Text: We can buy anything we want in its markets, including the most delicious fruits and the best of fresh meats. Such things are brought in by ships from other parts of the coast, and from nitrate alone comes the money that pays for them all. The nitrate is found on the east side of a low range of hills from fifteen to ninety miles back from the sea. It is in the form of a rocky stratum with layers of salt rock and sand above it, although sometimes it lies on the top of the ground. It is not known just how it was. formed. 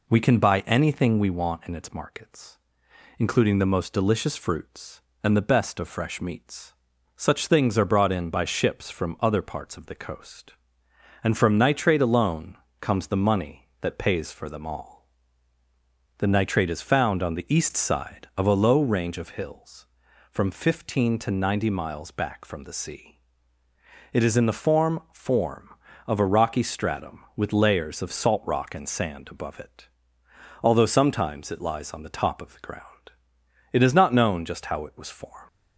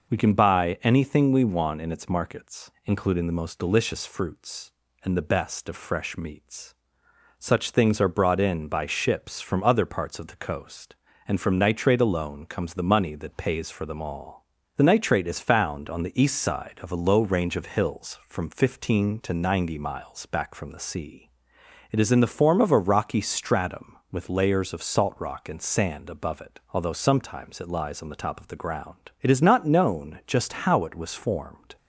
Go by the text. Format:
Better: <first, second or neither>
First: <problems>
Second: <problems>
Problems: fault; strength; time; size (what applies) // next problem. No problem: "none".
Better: second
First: pauses between "alone" and "comes"; slight; at 12.5 s; 0.24 s long // says "form" twice; at 25.1 s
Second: none